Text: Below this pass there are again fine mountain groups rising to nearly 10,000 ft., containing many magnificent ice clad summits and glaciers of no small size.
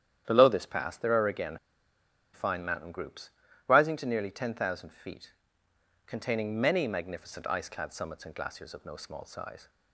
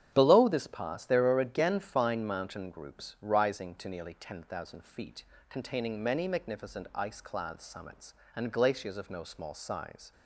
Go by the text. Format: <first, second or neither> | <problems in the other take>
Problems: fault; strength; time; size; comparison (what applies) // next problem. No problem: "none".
second | starts louder than the rest; strong; until 1.2 s; 10 dB; strong in the second // pauses between "again" and "fine"; noticeable; at 1.5 s; 0.77 s long // pauses between "groups" and "rising"; slight; at 3.3 s; 0.36 s long